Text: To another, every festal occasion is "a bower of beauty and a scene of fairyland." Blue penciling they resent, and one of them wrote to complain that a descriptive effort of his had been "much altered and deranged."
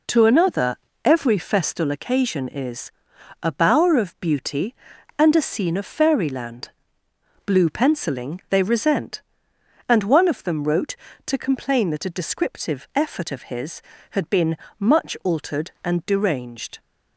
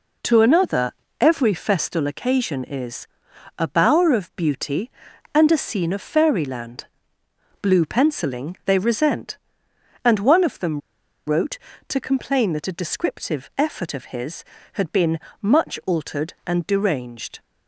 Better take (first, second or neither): first